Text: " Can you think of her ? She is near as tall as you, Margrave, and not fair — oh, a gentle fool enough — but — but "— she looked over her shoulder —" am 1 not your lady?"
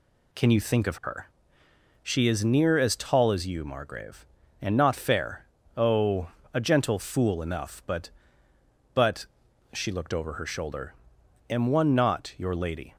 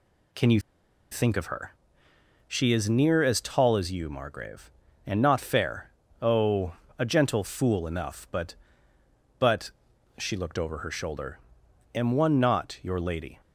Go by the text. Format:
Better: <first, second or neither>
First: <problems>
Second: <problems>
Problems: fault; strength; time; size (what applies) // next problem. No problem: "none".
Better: first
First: none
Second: pauses between "you" and "think"; noticeable; at 0.5 s; 0.52 s long